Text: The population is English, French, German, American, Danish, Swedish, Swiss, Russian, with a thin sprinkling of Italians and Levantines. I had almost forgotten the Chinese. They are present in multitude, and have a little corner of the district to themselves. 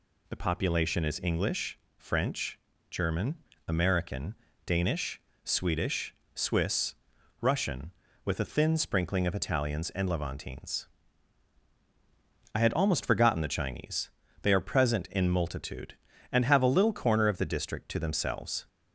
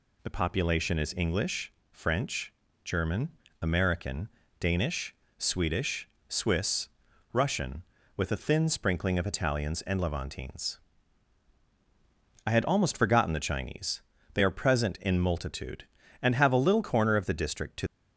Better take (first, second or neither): first